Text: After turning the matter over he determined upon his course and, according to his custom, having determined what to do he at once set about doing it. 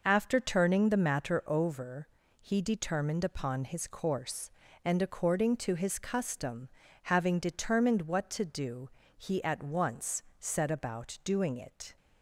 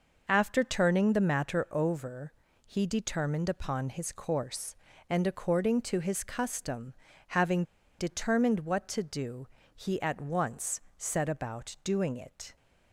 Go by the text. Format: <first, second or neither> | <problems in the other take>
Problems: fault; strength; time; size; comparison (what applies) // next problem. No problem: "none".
first | pauses between "over" and "he"; slight; at 2.3 s; 0.32 s long; slight in the first // pauses between "having" and "determined"; slight; at 7.6 s; 0.36 s long // pauses between "do" and "he"; slight; at 9.4 s; 0.30 s long; slight in the first // pauses between "once" and "set"; slight; at 10.7 s; 0.18 s long; slight in the first